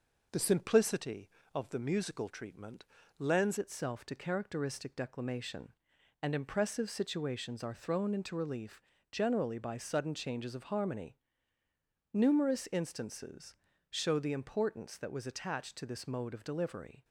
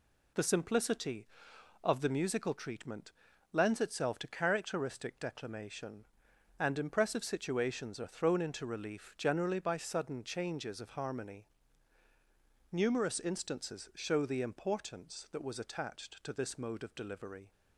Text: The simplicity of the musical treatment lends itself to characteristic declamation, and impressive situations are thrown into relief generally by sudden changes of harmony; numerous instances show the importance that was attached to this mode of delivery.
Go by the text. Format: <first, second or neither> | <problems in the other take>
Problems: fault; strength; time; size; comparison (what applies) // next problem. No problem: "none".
second | pauses between "treatment" and "lends"; slight; at 2.8 s; 0.32 s long; also in the second // changes voice at "itself"; from 3.5 s on; 13.5 s long // pauses between "relief" and "generally"; slight; at 8.8 s; 0.32 s long // pauses between "instances" and "show"; slight; at 13.5 s; 0.36 s long